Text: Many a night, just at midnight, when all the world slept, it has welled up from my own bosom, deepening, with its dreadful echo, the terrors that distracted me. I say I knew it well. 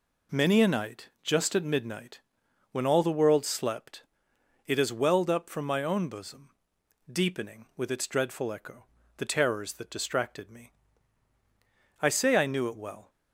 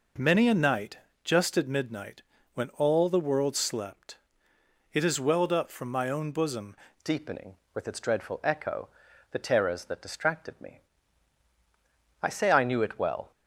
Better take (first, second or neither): first